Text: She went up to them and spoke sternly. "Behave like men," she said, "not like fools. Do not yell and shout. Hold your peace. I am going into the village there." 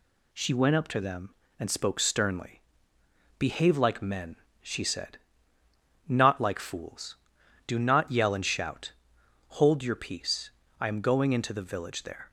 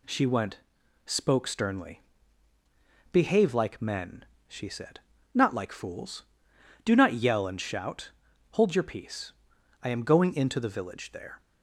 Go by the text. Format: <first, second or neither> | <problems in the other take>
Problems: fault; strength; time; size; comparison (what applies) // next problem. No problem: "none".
first | skips "up to them and"; at 0.8 s